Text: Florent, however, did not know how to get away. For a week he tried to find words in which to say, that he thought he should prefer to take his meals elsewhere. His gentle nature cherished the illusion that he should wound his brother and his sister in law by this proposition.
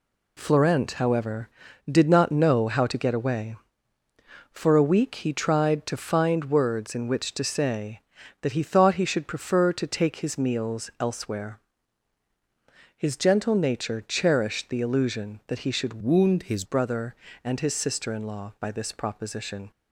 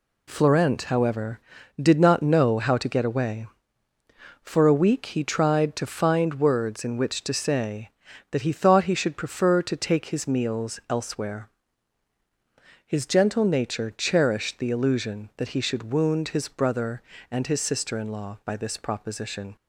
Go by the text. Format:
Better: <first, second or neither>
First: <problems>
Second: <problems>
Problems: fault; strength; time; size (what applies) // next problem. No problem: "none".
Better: second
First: changes voice from "wound" to "his"; from 16.0 to 16.6 s; 0.6 s long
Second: none